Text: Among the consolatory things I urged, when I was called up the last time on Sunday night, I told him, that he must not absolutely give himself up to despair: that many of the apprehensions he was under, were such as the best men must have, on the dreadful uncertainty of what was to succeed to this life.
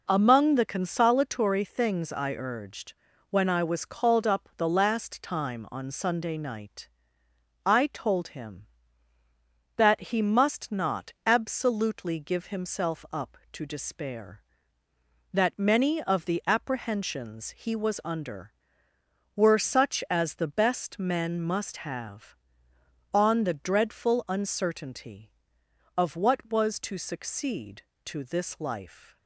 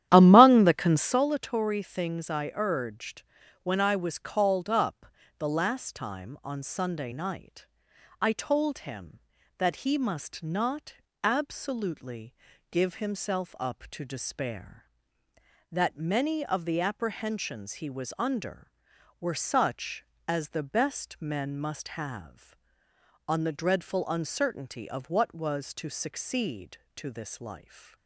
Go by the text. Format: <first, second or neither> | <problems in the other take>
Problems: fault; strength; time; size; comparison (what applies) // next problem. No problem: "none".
first | starts louder than the rest; strong; until 1.2 s; 11.5 dB // pauses between "up" and "the"; slight; at 5.0 s; 0.32 s long // pauses between "not" and "absolutely"; slight; at 10.9 s; 0.26 s long // pauses between "absolutely" and "give"; at 12.3 s; 0.38 s long